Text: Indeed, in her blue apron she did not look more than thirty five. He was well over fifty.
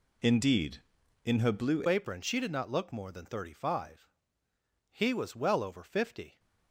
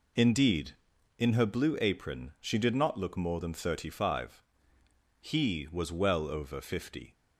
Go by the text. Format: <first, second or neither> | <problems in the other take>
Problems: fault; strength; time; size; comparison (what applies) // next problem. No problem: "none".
second | changes voice at "apron"; from 1.8 s on; 4.5 s long